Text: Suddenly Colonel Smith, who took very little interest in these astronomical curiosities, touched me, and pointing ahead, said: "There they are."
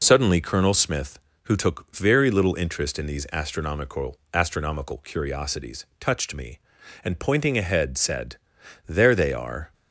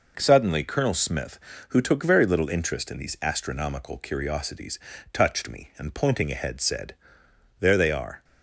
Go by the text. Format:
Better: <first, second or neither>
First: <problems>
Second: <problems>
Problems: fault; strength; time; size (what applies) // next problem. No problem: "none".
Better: second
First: says "astronomical" twice; at 4.3 s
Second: none